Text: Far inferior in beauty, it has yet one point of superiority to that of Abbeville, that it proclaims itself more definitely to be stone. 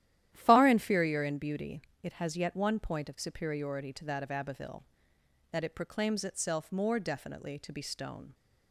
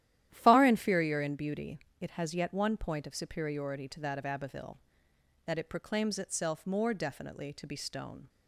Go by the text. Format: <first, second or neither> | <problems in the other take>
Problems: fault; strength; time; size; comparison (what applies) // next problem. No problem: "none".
neither | starts louder than the rest; strong; the same in both